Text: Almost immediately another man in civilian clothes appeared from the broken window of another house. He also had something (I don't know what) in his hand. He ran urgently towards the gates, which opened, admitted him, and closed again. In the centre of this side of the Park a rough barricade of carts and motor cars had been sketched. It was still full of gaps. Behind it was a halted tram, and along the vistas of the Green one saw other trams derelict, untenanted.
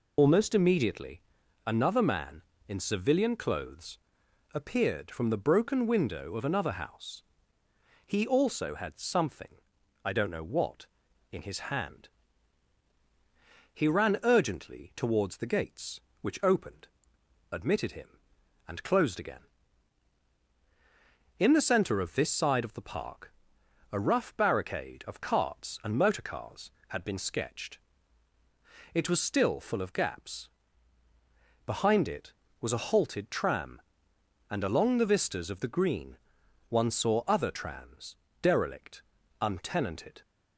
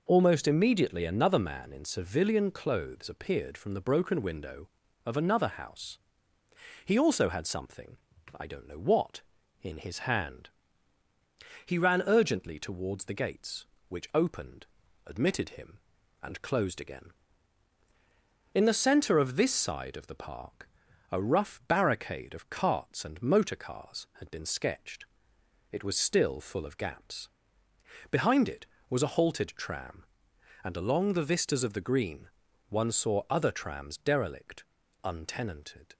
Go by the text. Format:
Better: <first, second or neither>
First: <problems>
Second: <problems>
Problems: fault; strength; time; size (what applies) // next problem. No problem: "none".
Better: second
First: loses the start of "Almost"; at 0.1 s; 65 ms // pauses between "immediately" and "another"; at 1.2 s; 0.44 s long // pauses between "clothes" and "appeared"; noticeable; at 3.9 s; 0.54 s long // pauses between "Park" and "a"; noticeable; at 23.3 s; 0.60 s long // pauses between "Green" and "one"; noticeable; at 36.1 s; 0.52 s long // pauses between "trams" and "derelict"; slight; at 38.1 s; 0.26 s long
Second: pauses between "Park" and "a"; at 20.6 s; 0.42 s long // pauses between "Green" and "one"; at 32.2 s; 0.40 s long